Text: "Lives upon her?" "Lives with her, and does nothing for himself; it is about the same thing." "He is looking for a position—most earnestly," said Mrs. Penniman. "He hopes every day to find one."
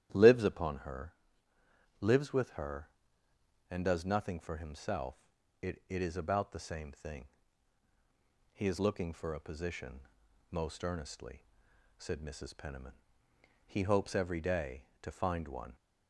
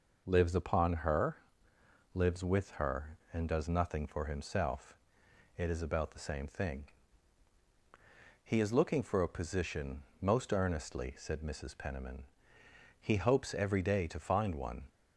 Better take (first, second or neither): second